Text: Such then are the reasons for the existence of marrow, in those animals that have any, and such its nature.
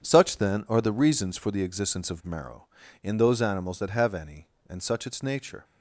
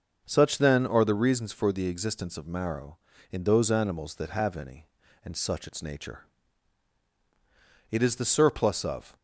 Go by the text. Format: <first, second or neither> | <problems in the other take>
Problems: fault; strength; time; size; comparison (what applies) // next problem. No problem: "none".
first | starts louder than the rest; until 1.2 s; 6.5 dB // goes on to say "It is the surplus of"; noticeable; from 7.9 s on; 1.2 s long